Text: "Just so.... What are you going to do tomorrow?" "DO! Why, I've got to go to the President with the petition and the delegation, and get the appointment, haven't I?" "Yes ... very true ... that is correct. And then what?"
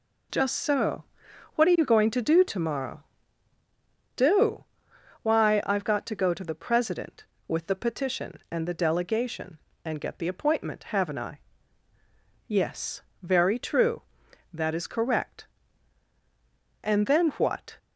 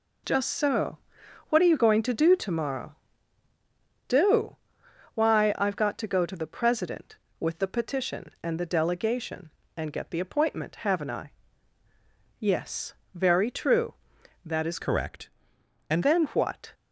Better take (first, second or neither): first